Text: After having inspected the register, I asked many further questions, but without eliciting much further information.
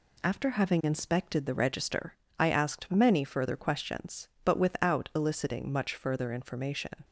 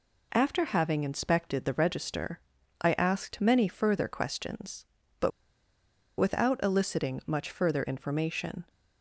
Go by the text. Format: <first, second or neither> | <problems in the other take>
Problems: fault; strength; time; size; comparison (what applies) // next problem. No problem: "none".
first | pauses between "but" and "without"; noticeable; at 5.3 s; 0.88 s long